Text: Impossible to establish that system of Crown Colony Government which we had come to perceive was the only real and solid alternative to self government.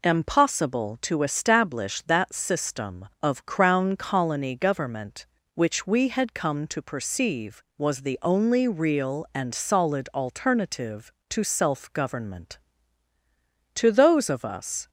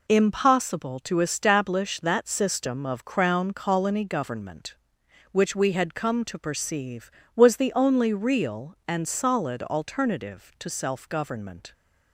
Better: second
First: goes on to say "To those of us"; noticeable; from 13.7 s on; 1.1 s long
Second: none

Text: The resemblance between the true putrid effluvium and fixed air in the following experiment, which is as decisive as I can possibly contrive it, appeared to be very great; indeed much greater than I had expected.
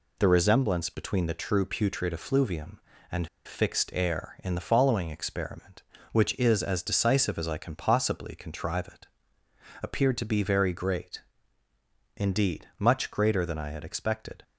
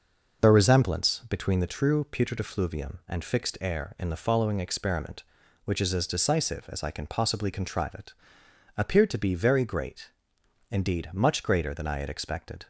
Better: second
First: pauses between "and" and "fixed"; slight; at 3.2 s; 0.17 s long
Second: none

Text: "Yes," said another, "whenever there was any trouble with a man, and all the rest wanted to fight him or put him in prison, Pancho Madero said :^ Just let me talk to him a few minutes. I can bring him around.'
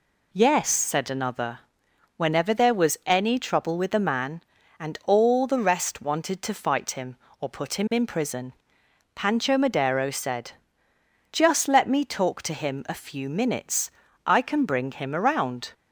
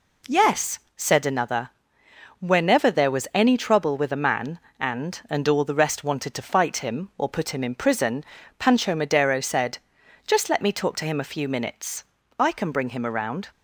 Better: first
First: none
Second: says "and" twice; at 5.2 s

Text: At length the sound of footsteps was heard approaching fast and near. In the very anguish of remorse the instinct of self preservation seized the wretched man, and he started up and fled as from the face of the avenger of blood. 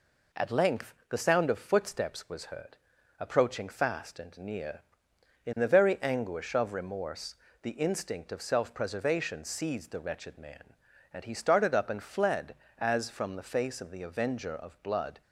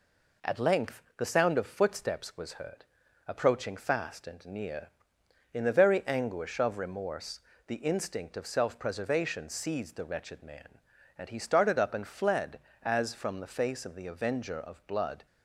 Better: neither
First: pauses between "length" and "the"; slight; at 0.9 s; 0.16 s long // pauses between "heard" and "approaching"; at 2.7 s; 0.42 s long // pauses between "remorse" and "the"; slight; at 7.3 s; 0.26 s long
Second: pauses between "length" and "the"; slight; at 1.0 s; 0.16 s long // pauses between "heard" and "approaching"; at 2.8 s; 0.42 s long // pauses between "remorse" and "the"; slight; at 7.3 s; 0.26 s long

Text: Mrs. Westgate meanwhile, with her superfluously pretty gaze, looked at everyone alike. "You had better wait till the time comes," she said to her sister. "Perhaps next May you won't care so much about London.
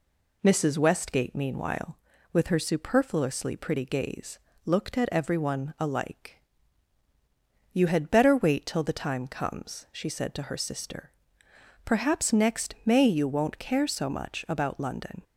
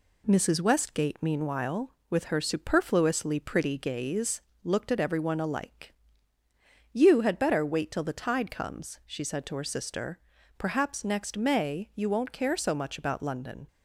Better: first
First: none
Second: says "tide" for "time"; at 8.2 s

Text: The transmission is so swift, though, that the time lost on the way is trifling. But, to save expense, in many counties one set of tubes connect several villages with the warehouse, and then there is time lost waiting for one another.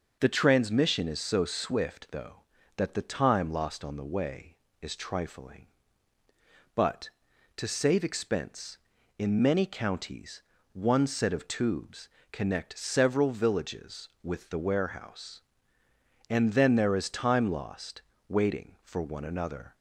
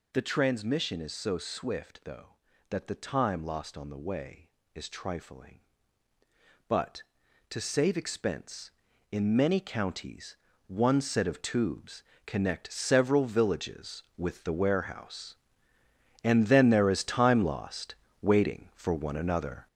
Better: first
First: pauses between "counties" and "one"; slight; at 10.4 s; 0.32 s long // pauses between "tubes" and "connect"; slight; at 12.0 s; 0.24 s long // pauses between "lost" and "waiting"; slight; at 18.0 s; 0.28 s long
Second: gets louder; throughout; 6.5 dB // pauses between "counties" and "one"; slight; at 10.3 s; 0.32 s long // pauses between "tubes" and "connect"; slight; at 12.0 s; 0.24 s long // pauses between "lost" and "waiting"; slight; at 17.9 s; 0.28 s long

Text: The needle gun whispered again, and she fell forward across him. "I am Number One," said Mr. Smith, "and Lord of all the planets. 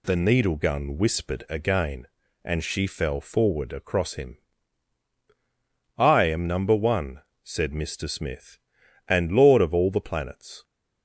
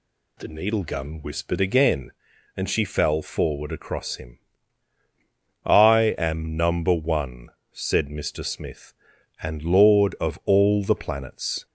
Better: neither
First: none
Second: none

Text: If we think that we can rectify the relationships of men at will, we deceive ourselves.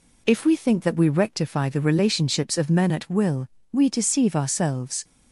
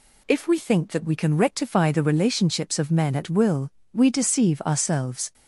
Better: second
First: skips "can"; at 1.0 s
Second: none

